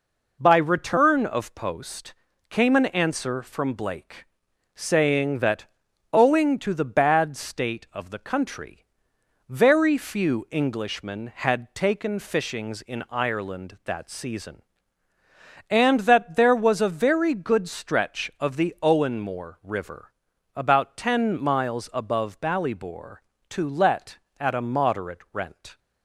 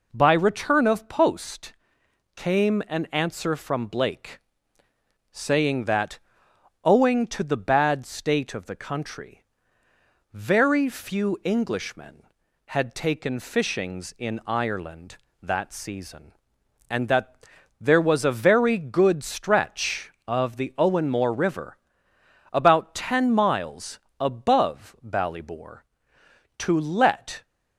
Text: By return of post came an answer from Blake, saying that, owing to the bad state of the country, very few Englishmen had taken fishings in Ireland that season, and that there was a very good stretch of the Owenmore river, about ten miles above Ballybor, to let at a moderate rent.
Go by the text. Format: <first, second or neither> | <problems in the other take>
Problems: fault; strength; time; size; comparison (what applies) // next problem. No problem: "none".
first | pauses between "post" and "came"; noticeable; at 1.7 s; 0.62 s long; slight in the first // pauses between "that" and "there"; at 17.3 s; 0.44 s long // pauses between "miles" and "above"; slight; at 23.9 s; 0.18 s long // stops before "at a moderate rent"; at 27.4 s